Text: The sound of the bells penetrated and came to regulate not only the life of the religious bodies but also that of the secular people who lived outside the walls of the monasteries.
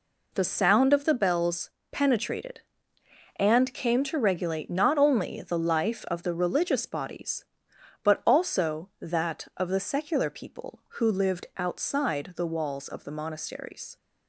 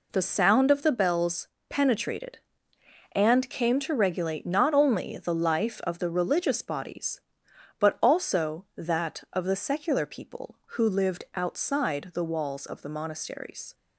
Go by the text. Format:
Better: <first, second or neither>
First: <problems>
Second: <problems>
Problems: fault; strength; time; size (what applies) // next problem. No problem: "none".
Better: neither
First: pauses between "bells" and "penetrated"; slight; at 1.6 s; 0.22 s long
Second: pauses between "bells" and "penetrated"; slight; at 1.4 s; 0.22 s long